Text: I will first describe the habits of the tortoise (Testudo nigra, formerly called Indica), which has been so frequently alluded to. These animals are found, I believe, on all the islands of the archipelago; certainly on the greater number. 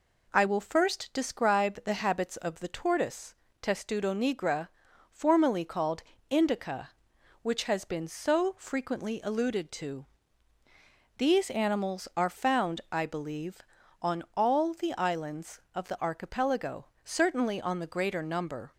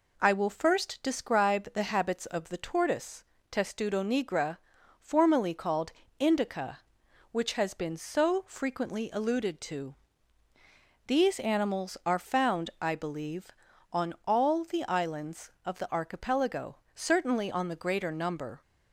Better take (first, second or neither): neither